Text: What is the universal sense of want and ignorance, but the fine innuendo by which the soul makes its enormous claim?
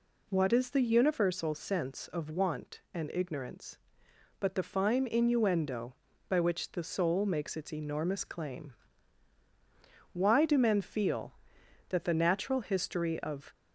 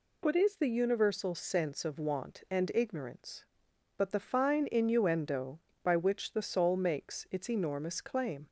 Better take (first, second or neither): second